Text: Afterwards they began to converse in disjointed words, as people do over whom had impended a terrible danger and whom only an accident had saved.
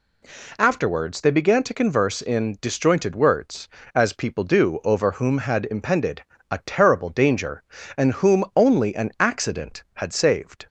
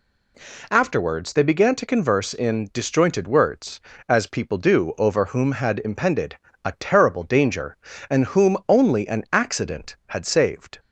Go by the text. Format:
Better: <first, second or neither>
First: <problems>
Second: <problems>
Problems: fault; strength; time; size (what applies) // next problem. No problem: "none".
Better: neither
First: pauses between "impended" and "a"; slight; at 6.2 s; 0.30 s long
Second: pauses between "impended" and "a"; slight; at 6.3 s; 0.30 s long